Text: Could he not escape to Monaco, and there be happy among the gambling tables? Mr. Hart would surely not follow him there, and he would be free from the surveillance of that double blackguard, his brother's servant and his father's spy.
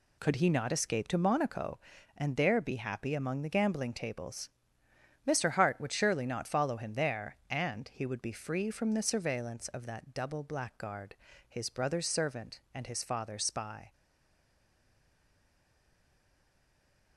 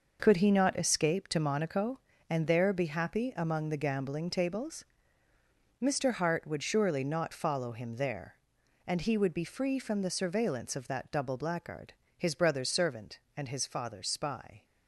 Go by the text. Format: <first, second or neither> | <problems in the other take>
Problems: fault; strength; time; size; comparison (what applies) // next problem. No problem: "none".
second | stays silent after the last word; strong; from 13.9 s on; 3.2 s long